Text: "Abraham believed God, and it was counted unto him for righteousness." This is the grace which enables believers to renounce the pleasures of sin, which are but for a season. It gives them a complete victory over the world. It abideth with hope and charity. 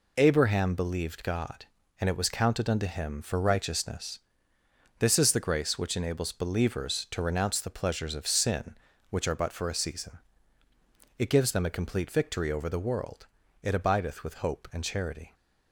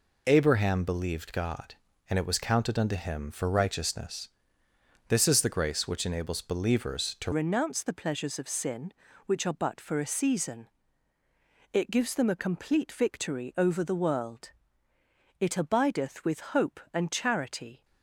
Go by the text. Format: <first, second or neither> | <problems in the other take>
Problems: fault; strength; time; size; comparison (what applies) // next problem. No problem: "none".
first | changes voice at "renounce"; from 7.3 s on; 10.5 s long